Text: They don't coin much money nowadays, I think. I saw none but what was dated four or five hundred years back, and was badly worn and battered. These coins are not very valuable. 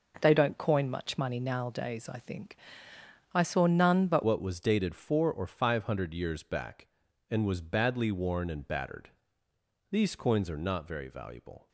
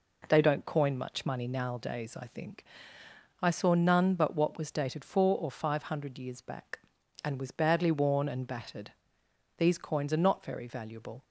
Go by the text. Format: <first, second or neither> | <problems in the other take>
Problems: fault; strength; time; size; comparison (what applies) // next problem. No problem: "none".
second | changes voice at "what"; from 4.2 s on; 7.4 s long